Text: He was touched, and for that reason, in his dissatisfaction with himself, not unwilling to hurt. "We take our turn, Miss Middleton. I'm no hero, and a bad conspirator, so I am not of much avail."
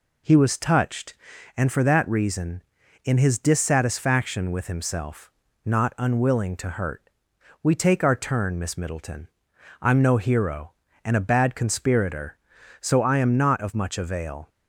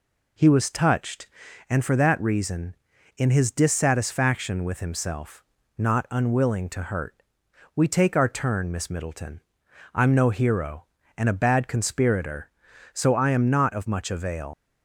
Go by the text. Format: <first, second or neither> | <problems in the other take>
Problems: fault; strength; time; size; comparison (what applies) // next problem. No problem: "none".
first | leaves "avail" unfinished; at 14.5 s; 80 ms